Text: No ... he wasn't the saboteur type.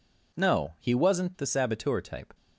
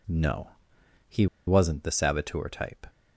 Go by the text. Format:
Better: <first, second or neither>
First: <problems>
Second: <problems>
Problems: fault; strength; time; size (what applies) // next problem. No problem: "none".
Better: first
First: none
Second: pauses between "he" and "wasn't"; slight; at 1.2 s; 0.21 s long